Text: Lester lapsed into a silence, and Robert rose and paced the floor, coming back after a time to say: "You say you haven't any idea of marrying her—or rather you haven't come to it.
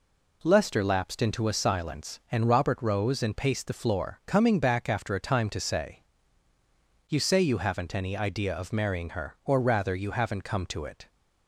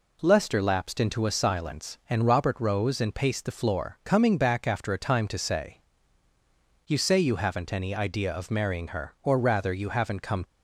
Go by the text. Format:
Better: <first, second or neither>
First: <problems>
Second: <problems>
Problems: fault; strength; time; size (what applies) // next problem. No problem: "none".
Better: first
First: none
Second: stops before "to it"; at 10.4 s